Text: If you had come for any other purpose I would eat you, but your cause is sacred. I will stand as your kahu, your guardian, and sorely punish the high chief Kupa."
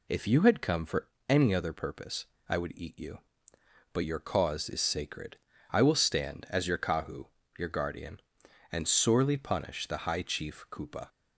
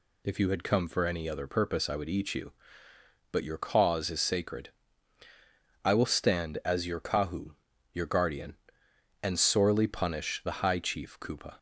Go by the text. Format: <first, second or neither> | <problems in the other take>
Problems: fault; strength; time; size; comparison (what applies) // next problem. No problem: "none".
second | loses the start of "If"; at 0.0 s; 40 ms // pauses between "for" and "any"; slight; at 1.0 s; 0.20 s long // pauses between "purpose" and "I"; slight; at 2.2 s; 0.22 s long